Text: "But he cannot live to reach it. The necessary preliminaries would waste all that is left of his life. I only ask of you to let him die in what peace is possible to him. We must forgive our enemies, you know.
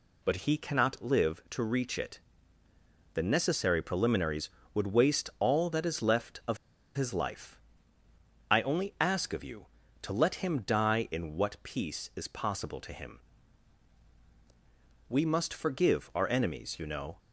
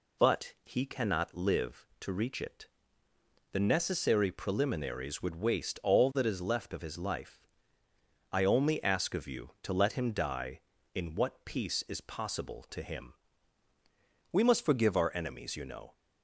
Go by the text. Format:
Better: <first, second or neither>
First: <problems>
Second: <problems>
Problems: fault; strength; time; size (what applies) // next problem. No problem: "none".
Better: second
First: pauses between "of" and "his"; at 6.5 s; 0.39 s long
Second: none